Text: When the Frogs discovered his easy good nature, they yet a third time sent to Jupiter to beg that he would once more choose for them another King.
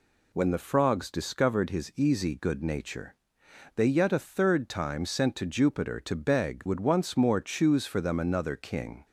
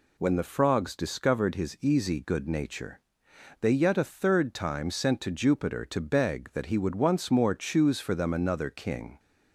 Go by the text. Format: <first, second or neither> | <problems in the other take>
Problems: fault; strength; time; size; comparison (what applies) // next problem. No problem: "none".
second | skips "that he"; at 6.6 s